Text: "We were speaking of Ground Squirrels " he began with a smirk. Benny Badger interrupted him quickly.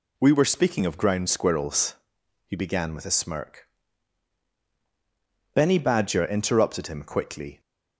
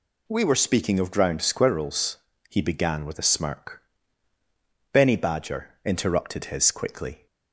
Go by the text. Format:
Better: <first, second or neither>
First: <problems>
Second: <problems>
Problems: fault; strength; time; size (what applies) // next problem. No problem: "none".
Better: first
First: none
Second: says "his" for "him"; at 6.4 s